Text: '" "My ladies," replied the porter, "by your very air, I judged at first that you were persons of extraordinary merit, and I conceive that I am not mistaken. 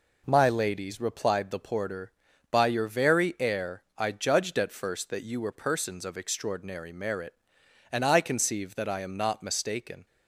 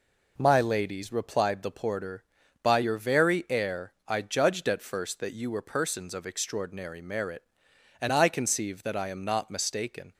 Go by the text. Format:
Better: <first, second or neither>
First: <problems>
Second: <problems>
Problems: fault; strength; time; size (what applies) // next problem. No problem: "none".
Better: neither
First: none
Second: none